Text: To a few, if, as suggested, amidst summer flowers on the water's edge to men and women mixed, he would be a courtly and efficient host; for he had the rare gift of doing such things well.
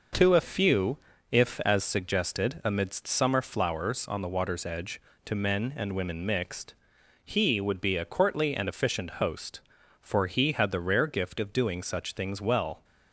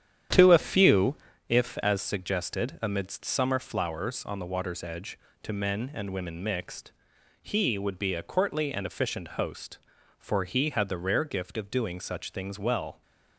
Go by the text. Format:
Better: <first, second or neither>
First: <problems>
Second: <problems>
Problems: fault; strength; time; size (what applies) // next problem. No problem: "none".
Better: first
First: none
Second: starts louder than the rest; strong; until 1.4 s; 9.5 dB